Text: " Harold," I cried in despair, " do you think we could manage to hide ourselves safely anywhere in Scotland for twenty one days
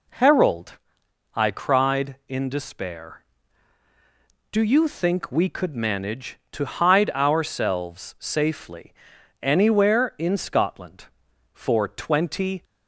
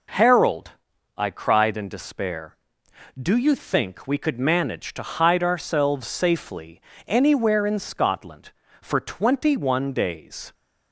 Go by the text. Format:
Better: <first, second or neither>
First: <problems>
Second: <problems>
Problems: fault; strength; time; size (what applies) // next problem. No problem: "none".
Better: second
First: pauses between "safely" and "anywhere"; noticeable; at 8.9 s; 0.48 s long // stops before "one days"; at 12.6 s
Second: pauses between "safely" and "anywhere"; slight; at 6.8 s; 0.24 s long